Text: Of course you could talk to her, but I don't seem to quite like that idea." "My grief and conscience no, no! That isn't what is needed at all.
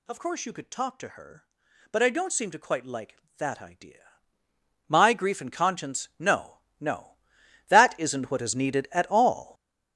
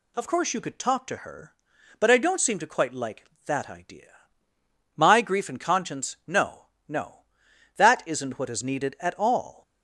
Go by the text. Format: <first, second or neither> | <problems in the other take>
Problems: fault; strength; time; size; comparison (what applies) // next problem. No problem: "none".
second | gets louder; strong; throughout; 10 dB